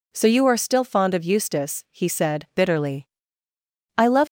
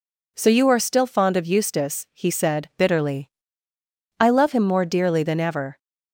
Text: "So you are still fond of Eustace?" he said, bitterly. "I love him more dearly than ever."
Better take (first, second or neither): second